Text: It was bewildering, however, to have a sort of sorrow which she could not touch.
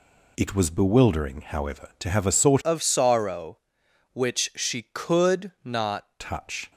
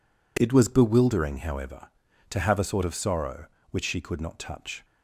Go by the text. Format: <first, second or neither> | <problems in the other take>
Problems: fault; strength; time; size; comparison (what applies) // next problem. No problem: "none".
second | changes voice from "of" to "not"; from 2.6 to 6.0 s; 3.4 s long